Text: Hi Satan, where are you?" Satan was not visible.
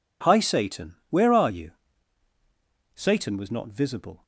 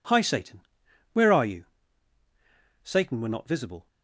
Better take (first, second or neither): first